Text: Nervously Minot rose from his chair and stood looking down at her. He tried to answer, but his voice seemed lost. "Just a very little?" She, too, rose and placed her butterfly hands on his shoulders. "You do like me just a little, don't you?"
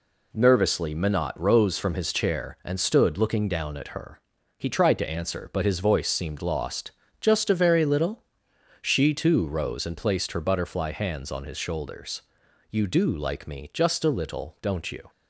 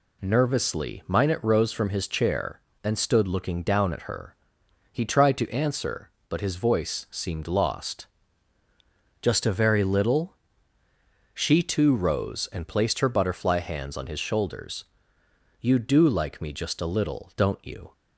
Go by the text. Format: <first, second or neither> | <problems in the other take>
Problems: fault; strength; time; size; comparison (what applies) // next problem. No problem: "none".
neither | none